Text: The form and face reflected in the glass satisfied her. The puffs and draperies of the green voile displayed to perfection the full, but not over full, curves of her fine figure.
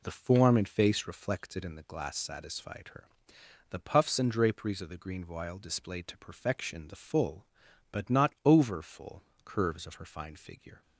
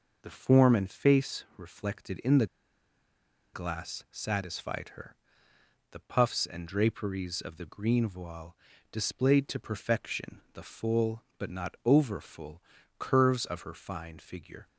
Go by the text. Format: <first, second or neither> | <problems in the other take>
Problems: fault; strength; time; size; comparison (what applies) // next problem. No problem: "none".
first | pauses between "the" and "glass"; at 2.4 s; 1.0 s long // pauses between "voile" and "displayed"; at 8.5 s; 0.38 s long